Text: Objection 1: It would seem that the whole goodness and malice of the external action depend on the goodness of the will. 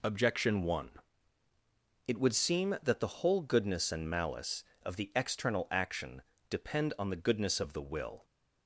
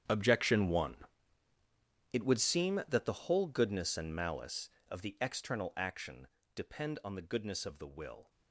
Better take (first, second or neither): first